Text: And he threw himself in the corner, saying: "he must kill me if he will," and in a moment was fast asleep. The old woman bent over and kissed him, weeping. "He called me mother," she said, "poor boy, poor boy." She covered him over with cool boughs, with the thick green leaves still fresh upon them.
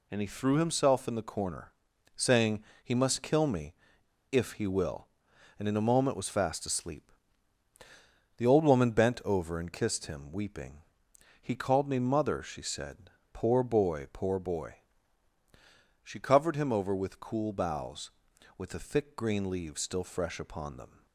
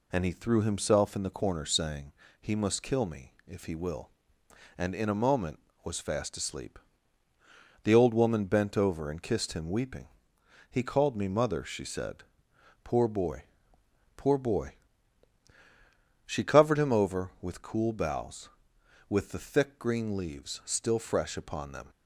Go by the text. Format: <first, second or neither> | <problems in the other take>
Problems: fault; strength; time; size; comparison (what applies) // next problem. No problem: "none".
second | pauses between "me" and "if"; noticeable; at 3.7 s; 0.57 s long